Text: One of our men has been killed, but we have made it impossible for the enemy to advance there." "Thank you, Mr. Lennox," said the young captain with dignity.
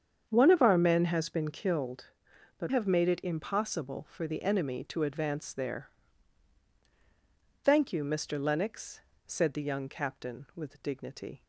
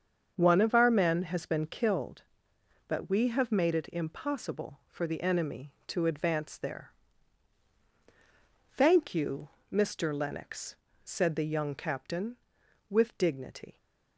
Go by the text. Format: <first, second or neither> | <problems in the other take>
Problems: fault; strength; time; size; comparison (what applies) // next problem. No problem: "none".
second | starts louder than the rest; strong; until 1.3 s; 7.5 dB; also in the second // skips "we"; at 2.6 s